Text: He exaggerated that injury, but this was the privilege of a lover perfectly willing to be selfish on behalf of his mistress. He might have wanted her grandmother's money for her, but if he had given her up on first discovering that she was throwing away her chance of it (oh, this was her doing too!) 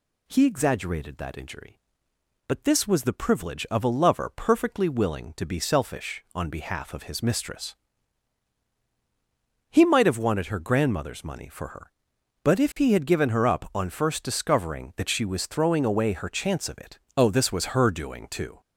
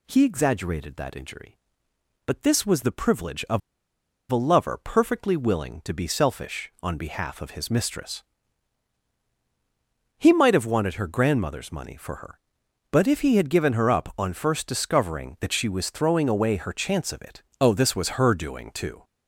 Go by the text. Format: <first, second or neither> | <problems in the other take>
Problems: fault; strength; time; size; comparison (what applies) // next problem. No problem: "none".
first | pauses between "of" and "a"; noticeable; at 3.6 s; 0.71 s long